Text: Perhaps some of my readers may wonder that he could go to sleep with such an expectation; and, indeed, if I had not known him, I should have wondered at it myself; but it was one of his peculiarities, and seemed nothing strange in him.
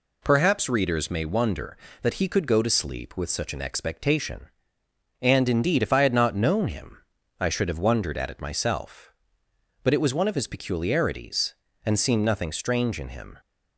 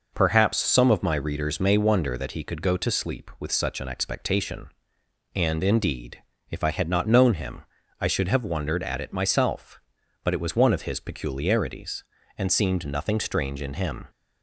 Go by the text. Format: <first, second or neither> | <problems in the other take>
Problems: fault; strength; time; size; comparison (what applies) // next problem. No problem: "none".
second | skips "some of my"; at 0.6 s